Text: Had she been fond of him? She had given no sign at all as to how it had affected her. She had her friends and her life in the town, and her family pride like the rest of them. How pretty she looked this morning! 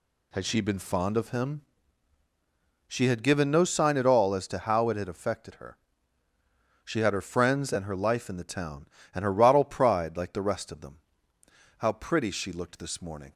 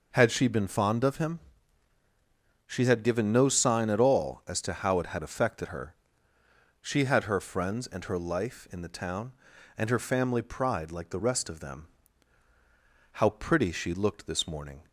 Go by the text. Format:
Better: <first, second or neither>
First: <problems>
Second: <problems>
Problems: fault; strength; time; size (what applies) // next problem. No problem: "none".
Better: second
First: says "rottle" for "family"; at 9.3 s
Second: none